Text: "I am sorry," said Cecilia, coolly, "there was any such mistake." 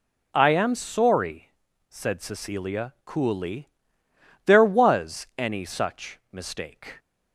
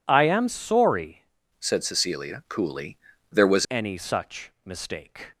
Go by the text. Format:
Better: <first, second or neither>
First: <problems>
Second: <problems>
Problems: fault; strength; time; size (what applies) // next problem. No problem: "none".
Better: first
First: none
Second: changes voice from "said" to "was"; from 1.6 to 3.6 s; 2.0 s long